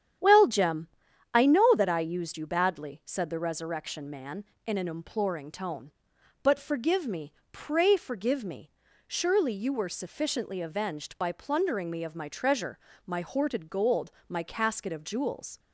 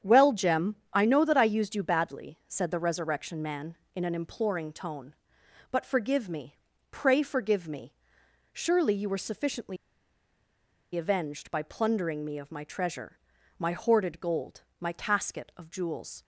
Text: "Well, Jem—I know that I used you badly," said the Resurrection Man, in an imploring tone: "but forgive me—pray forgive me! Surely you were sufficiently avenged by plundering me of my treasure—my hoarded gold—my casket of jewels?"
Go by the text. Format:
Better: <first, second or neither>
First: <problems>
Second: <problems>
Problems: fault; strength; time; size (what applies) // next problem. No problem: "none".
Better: first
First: starts louder than the rest; strong; until 1.6 s; 9.5 dB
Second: starts louder than the rest; strong; until 1.2 s; 8.5 dB // pauses between "sufficiently" and "avenged"; at 9.7 s; 1.1 s long